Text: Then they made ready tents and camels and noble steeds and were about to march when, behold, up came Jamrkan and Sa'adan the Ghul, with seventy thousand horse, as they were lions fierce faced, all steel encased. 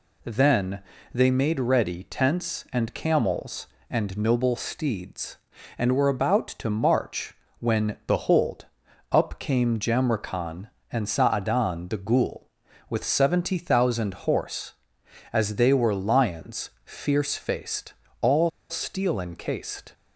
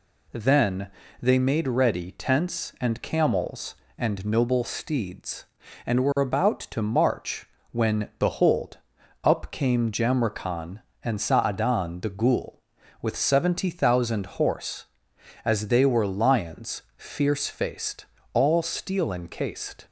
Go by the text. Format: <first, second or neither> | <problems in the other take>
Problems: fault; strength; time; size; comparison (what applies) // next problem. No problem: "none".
second | pauses between "Then" and "they"; slight; at 0.8 s; 0.32 s long; slight in the second // pauses between "march" and "when"; slight; at 7.3 s; 0.26 s long; slight in the second // pauses between "lions" and "fierce"; slight; at 16.6 s; 0.16 s long; slight in the second // pauses between "all" and "steel"; slight; at 18.4 s; 0.20 s long